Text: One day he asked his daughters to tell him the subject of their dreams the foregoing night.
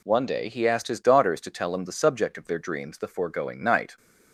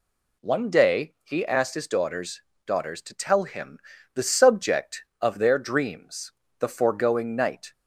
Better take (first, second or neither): first